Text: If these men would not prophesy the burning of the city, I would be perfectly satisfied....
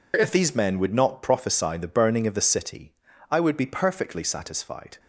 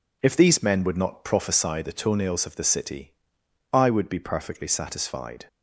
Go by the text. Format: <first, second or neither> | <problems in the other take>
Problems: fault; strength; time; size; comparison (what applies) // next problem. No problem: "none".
first | says "toenails" for "burning"; at 1.9 s